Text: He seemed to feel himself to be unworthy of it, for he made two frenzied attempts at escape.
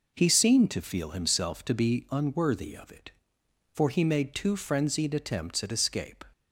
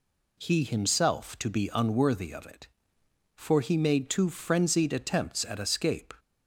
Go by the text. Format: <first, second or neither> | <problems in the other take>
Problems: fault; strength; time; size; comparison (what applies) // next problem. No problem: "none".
first | skips "seemed to feel"; at 0.6 s